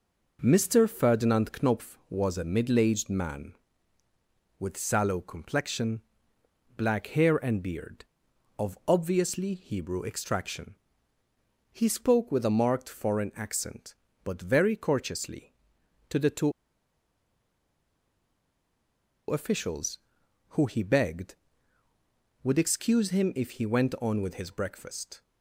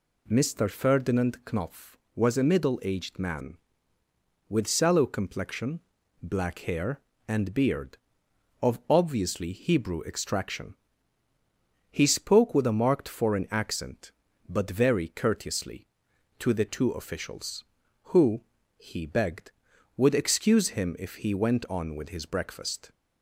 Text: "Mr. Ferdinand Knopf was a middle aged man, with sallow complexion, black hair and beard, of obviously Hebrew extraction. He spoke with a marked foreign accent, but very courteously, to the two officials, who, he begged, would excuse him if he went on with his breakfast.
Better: second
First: pauses between "two" and "officials"; strong; at 16.5 s; 2.7 s long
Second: none

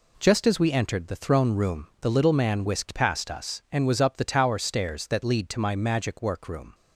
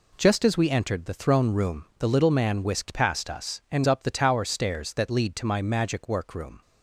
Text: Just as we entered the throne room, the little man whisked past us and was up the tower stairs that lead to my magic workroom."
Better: first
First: none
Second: skips "was"; at 3.8 s

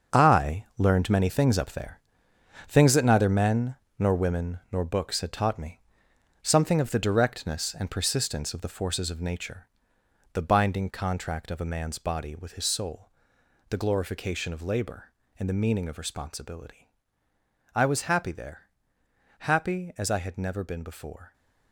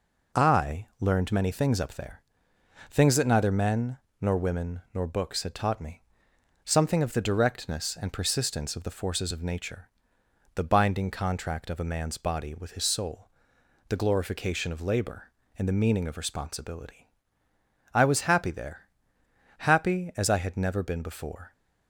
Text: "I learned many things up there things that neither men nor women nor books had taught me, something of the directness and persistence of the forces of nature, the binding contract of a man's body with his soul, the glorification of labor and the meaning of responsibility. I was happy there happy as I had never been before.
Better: second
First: gets quieter; strong; throughout; 10 dB // pauses between "there" and "things"; noticeable; at 2.0 s; 0.66 s long // pauses between "men" and "nor"; slight; at 3.7 s; 0.22 s long // pauses between "there" and "happy"; noticeable; at 18.6 s; 0.70 s long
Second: pauses between "there" and "things"; noticeable; at 2.2 s; 0.66 s long // pauses between "men" and "nor"; slight; at 3.9 s; 0.22 s long // pauses between "there" and "happy"; noticeable; at 18.8 s; 0.70 s long

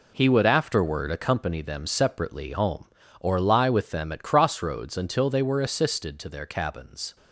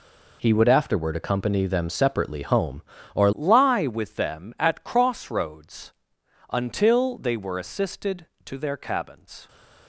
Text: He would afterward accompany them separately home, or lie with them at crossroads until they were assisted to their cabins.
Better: first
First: none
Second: changes voice at "lie"; from 3.3 s on; 6.1 s long // pauses between "crossroads" and "until"; noticeable; at 5.9 s; 0.58 s long

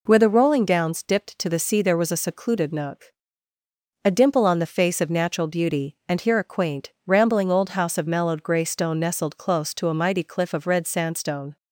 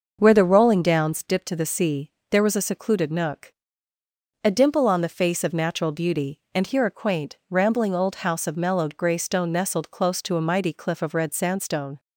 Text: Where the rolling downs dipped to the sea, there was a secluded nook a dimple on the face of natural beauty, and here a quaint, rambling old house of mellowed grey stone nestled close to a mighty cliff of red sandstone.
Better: first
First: pauses between "nook" and "a"; noticeable; at 3.1 s; 0.92 s long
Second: starts louder than the rest; noticeable; until 1.2 s; 6 dB // pauses between "nook" and "a"; noticeable; at 3.5 s; 0.90 s long

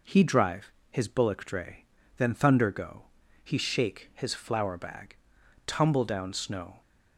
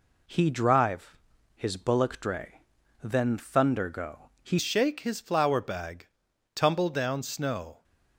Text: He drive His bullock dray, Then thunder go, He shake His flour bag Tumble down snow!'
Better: first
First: pauses between "drive" and "His"; slight; at 0.6 s; 0.20 s long // pauses between "bag" and "Tumble"; noticeable; at 5.1 s; 0.50 s long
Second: pauses between "drive" and "His"; at 1.1 s; 0.38 s long // changes voice at "shake"; from 4.5 s on; 3.3 s long // pauses between "bag" and "Tumble"; noticeable; at 6.0 s; 0.46 s long

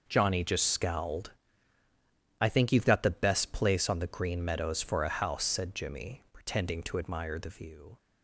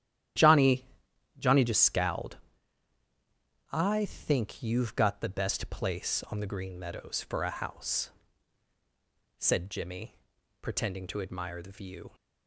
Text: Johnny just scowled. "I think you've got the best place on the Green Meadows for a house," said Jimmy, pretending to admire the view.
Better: first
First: none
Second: starts louder than the rest; strong; until 1.9 s; 11.5 dB // says "Johnny" twice; at 1.3 s

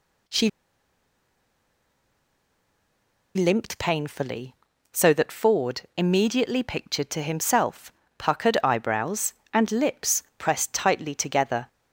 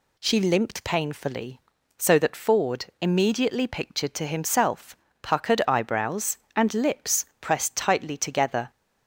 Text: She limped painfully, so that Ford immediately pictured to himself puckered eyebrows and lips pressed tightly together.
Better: second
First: pauses between "She" and "limped"; strong; at 0.4 s; 2.8 s long // pauses between "Ford" and "immediately"; slight; at 5.8 s; 0.16 s long // pauses between "himself" and "puckered"; slight; at 7.9 s; 0.26 s long // pauses between "lips" and "pressed"; slight; at 10.2 s; 0.16 s long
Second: pauses between "Ford" and "immediately"; slight; at 2.8 s; 0.16 s long // pauses between "himself" and "puckered"; slight; at 4.9 s; 0.26 s long // pauses between "lips" and "pressed"; slight; at 7.2 s; 0.16 s long

